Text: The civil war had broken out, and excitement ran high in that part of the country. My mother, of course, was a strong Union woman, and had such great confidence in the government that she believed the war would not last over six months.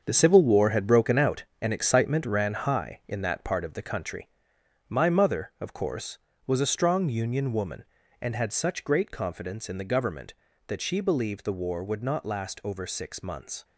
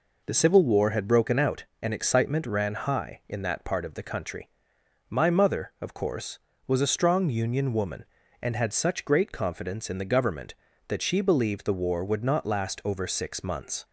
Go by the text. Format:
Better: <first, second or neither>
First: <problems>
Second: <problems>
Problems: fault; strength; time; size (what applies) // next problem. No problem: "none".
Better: second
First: gets quieter; strong; throughout; 9 dB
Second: none